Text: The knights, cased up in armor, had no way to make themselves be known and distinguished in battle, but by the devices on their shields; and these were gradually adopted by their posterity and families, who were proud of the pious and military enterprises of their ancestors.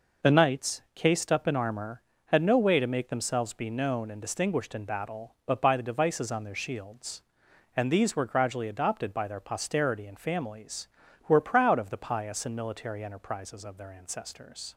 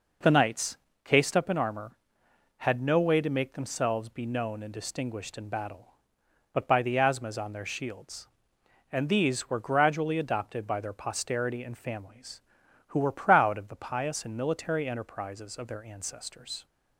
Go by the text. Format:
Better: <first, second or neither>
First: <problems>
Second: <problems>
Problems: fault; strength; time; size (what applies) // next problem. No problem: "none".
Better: first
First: none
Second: says "asthmas" for "devices"; at 6.9 s